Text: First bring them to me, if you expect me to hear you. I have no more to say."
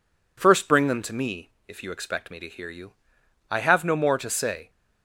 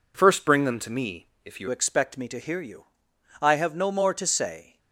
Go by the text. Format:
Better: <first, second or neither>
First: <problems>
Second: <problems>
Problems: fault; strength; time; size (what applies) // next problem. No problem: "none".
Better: first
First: none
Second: changes voice at "expect"; from 1.6 s on; 3.1 s long